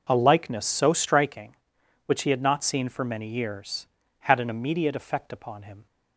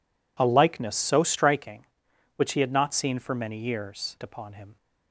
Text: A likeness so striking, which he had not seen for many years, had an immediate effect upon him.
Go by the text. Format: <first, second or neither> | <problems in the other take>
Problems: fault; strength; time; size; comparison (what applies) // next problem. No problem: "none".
first | skips "had an immediate effect"; at 4.2 s